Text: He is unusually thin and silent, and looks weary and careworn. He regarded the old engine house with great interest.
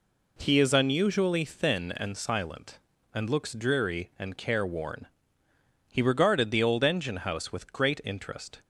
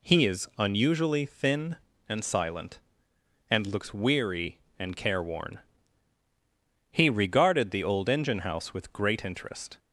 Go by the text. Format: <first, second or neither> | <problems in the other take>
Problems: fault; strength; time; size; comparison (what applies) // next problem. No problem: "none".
second | says "dreary" for "weary"; at 3.5 s